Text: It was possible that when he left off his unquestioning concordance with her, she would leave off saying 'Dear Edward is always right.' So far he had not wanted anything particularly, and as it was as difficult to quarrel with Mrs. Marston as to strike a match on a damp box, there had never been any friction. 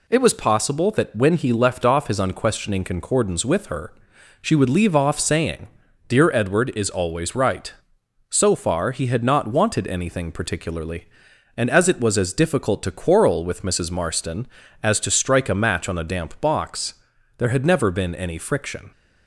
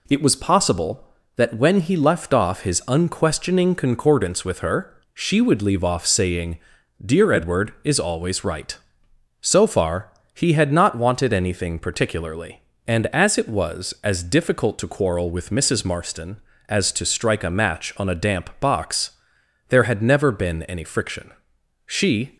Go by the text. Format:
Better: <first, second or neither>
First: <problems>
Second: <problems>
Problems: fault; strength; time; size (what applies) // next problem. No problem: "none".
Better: first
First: pauses between "saying" and "Dear"; at 5.6 s; 0.40 s long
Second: pauses between "saying" and "Dear"; noticeable; at 6.5 s; 0.46 s long // pauses between "far" and "he"; slight; at 10.1 s; 0.20 s long // goes on to say "She"; from 21.8 s on; 0.52 s long